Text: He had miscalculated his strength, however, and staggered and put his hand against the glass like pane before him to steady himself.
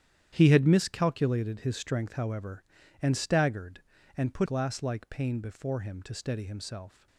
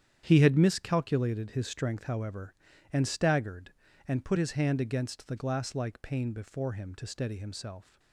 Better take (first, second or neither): second